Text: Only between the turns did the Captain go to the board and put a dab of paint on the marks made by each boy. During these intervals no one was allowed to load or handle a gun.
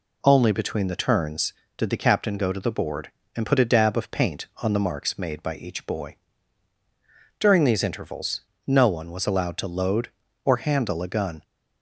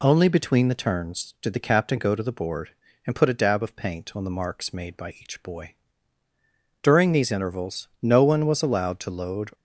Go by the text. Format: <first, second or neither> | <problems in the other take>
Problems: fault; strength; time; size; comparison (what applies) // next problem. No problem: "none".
first | pauses between "intervals" and "no"; slight; at 7.8 s; 0.16 s long; slight in the first // stops before "or handle a gun"; at 9.5 s